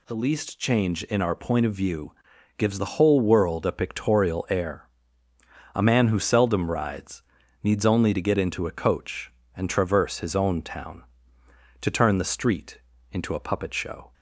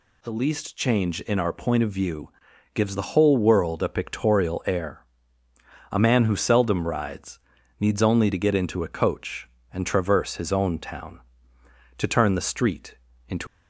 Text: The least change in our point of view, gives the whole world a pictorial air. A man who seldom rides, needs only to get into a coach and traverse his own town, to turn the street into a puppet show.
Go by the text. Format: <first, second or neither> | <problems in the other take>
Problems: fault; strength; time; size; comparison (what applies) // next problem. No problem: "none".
first | pauses between "street" and "into"; slight; at 12.9 s; 0.34 s long; slight in the first // stops before "a puppet show"; at 13.4 s